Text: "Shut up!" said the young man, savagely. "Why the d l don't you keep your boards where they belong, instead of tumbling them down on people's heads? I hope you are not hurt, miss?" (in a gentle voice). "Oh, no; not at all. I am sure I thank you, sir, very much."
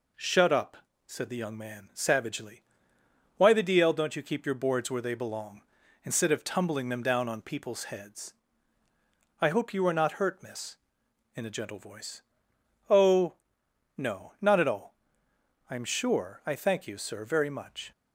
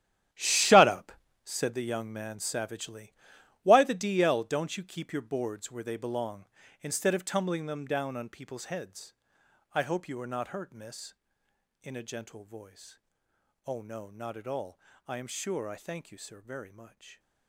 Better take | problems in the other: first | gets quieter; strong; throughout; 13 dB

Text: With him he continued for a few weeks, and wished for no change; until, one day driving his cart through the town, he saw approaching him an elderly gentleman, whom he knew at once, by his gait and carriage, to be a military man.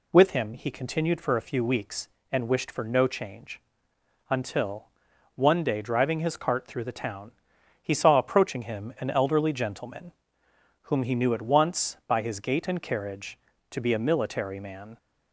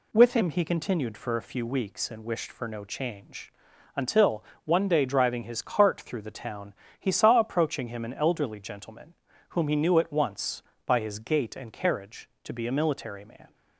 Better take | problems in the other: neither | none

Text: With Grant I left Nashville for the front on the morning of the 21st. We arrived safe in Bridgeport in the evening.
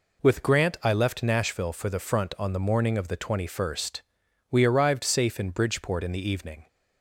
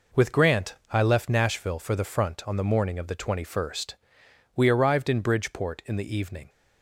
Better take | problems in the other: first | pauses between "Grant" and "I"; slight; at 0.7 s; 0.18 s long // skips "safe"; at 5.0 s

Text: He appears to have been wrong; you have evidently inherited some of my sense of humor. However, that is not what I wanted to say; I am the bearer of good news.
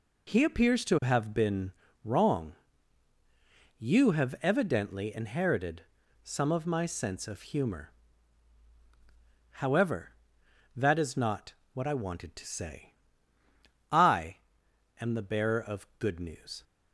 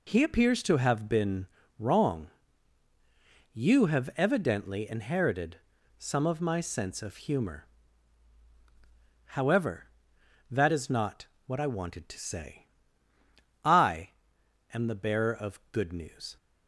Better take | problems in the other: neither | pauses between "been" and "wrong"; slight; the same in both // pauses between "inherited" and "some"; the same in both // pauses between "not" and "what"; slight; the same in both // pauses between "I" and "am"; noticeable; the same in both

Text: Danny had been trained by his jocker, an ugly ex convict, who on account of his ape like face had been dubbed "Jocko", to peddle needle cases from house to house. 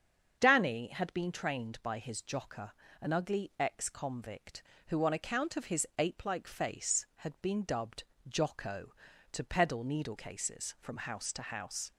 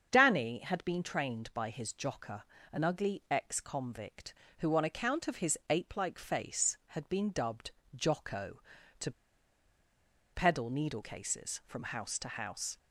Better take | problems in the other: first | starts louder than the rest; until 1.1 s; 7 dB; strong in the first // pauses between "dubbed" and "Jocko"; slight; at 7.6 s; 0.26 s long; slight in the first // pauses between "to" and "peddle"; at 9.1 s; 1.2 s long

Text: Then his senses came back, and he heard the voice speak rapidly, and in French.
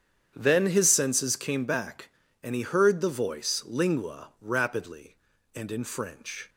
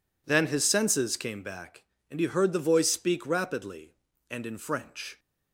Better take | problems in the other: second | starts louder than the rest; strong; until 1.3 s; 8.5 dB // says "lingua" for "speak"; at 3.6 s

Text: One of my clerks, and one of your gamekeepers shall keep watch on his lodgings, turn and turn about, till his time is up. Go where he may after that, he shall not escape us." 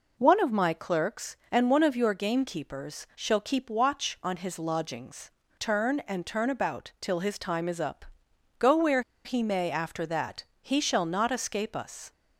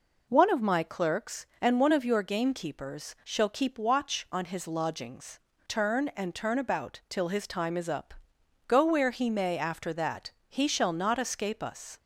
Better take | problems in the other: second | pauses between "where" and "he"; slight; at 9.0 s; 0.23 s long

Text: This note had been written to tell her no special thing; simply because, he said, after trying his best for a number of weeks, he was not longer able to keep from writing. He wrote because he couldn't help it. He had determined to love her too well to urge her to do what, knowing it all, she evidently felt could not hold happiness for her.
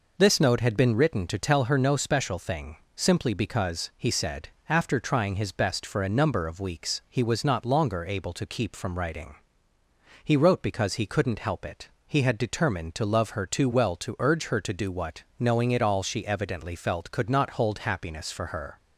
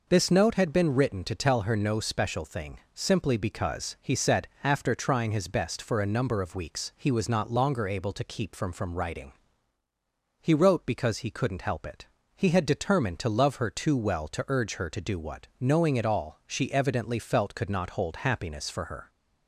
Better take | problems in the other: first | says "from" twice; at 8.7 s

